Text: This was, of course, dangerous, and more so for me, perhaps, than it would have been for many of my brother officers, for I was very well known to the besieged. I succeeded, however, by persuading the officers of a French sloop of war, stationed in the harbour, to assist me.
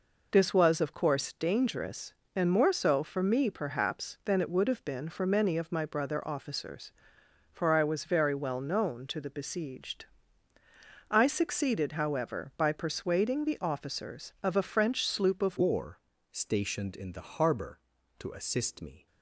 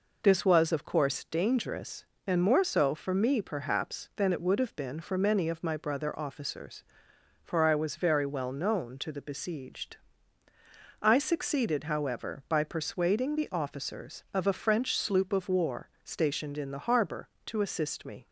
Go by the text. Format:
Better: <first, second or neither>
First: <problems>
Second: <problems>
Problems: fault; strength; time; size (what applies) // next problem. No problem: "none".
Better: second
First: changes voice at "war"; from 15.5 s on; 3.5 s long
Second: none